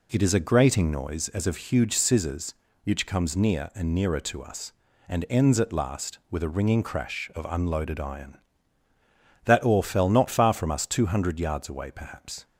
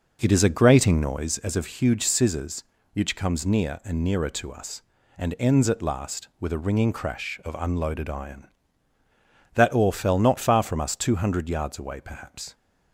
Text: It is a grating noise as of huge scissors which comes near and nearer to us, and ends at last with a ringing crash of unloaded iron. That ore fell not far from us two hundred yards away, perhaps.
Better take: first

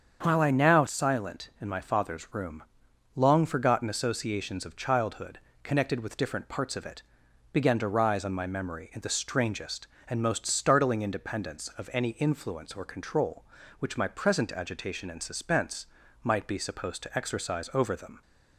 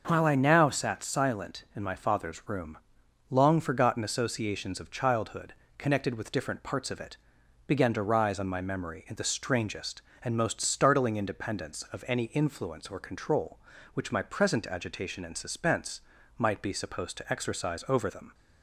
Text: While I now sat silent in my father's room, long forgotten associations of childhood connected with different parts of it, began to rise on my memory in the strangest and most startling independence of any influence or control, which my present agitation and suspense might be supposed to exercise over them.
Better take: second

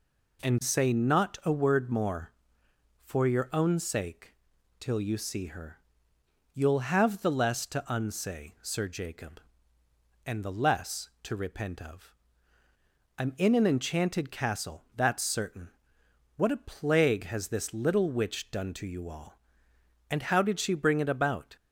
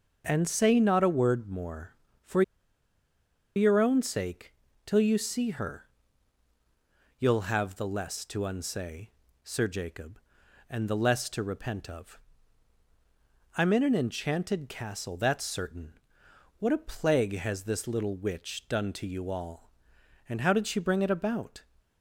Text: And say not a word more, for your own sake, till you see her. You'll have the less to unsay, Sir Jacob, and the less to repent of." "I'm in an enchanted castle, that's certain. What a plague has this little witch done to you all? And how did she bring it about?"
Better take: first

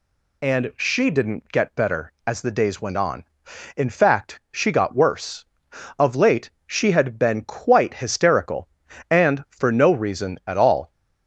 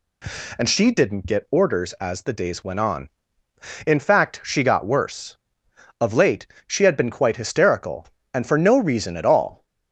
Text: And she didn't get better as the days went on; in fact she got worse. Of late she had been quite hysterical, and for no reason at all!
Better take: first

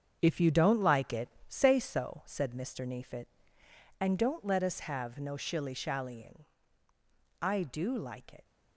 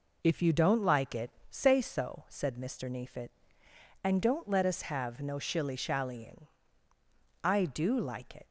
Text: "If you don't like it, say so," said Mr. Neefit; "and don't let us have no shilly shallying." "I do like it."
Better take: second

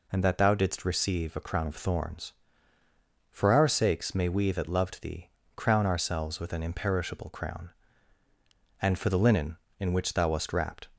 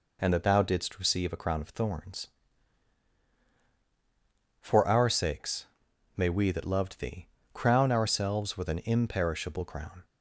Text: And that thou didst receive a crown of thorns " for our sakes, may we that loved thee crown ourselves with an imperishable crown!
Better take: second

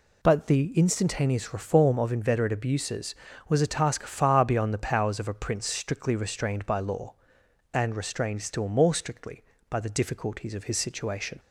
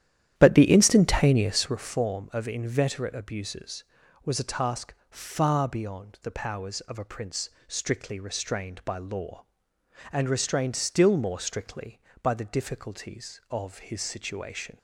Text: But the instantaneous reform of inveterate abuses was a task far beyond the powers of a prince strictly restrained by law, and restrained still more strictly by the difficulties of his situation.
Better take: first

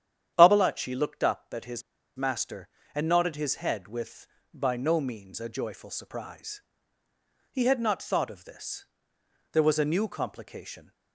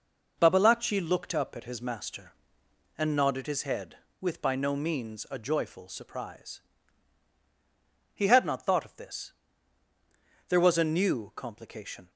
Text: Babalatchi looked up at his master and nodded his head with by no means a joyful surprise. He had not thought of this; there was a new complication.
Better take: second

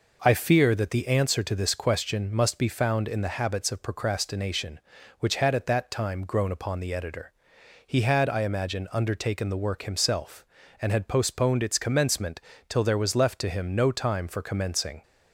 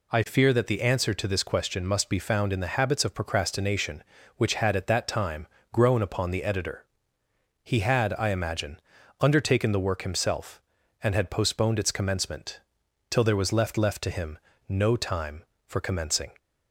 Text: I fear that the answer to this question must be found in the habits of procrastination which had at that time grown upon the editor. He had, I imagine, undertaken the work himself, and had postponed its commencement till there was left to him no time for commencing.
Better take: first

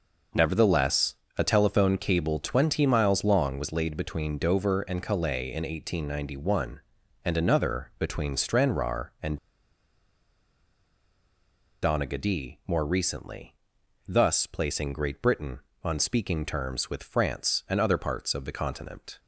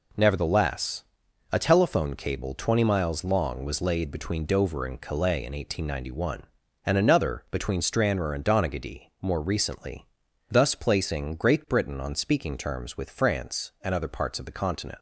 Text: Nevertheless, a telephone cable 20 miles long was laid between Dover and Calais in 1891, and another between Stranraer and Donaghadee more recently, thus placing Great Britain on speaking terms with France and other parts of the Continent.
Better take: second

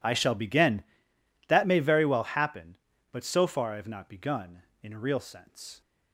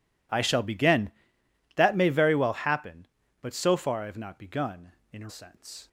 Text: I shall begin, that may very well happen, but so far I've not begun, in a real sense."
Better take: first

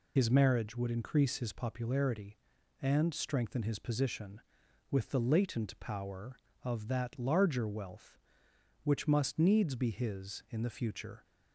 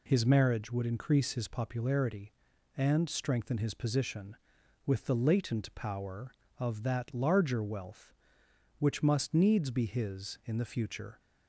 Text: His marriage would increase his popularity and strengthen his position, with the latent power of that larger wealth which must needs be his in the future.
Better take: second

